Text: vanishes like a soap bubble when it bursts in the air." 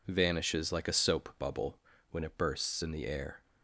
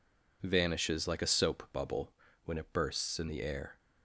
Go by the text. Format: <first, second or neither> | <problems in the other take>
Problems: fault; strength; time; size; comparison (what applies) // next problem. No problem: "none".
neither | pauses between "bubble" and "when"; slight; the same in both